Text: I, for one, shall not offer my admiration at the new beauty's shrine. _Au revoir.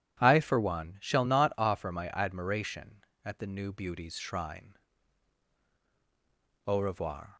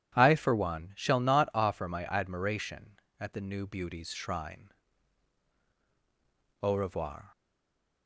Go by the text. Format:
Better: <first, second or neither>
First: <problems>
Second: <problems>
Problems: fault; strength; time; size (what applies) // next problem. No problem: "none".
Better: first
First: none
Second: stays silent after the last word; slight; from 7.3 s on; 0.7 s long